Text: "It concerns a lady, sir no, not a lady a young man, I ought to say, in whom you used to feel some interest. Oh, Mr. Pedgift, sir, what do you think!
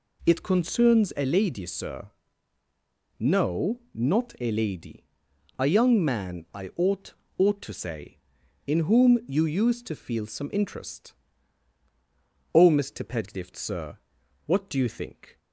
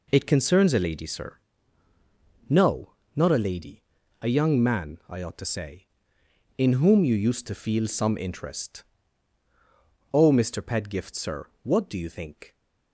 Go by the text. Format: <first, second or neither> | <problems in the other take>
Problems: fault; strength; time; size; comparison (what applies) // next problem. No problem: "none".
second | pauses between "sir" and "no"; at 2.1 s; 1.1 s long; also in the second // pauses between "lady" and "a"; noticeable; at 5.0 s; 0.54 s long; also in the second // says "ought" twice; at 7.3 s